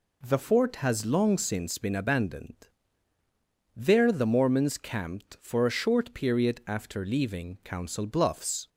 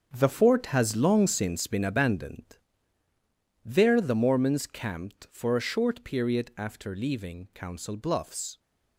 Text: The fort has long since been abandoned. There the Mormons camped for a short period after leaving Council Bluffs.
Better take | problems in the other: first | gets quieter; strong; throughout; 10.5 dB

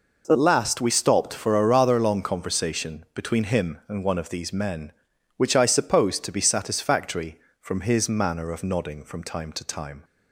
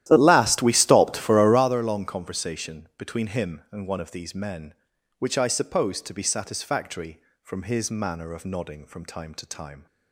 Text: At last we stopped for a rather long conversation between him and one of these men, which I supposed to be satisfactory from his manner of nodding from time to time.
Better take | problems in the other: first | starts louder than the rest; strong; until 1.7 s; 13 dB

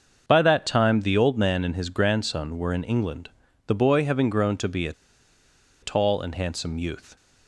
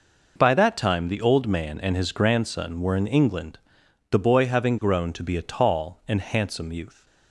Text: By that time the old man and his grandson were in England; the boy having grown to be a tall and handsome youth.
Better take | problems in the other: second | starts louder than the rest; until 1.2 s; 6.5 dB // pauses between "a" and "tall"; noticeable; at 4.9 s; 0.90 s long

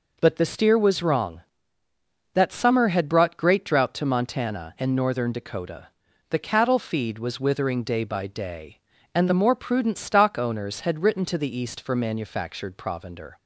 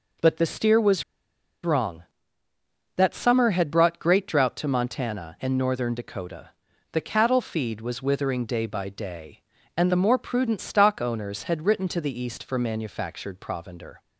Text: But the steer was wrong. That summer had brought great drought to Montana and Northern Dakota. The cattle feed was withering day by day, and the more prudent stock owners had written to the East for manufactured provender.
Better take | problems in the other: first | pauses between "was" and "wrong"; noticeable; at 1.0 s; 0.60 s long

